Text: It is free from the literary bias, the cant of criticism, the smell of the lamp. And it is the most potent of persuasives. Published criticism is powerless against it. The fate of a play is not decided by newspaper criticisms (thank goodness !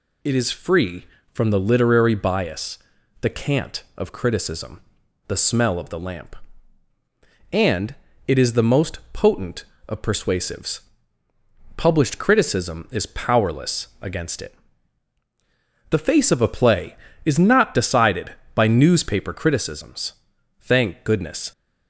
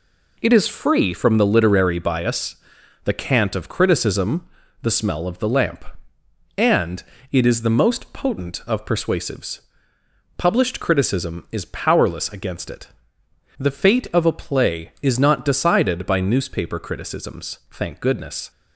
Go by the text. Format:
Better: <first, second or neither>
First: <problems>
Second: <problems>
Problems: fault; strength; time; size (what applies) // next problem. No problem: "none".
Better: second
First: pauses between "And" and "it"; slight; at 7.9 s; 0.34 s long // says "face" for "fate"; at 15.9 s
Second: pauses between "And" and "it"; slight; at 7.0 s; 0.28 s long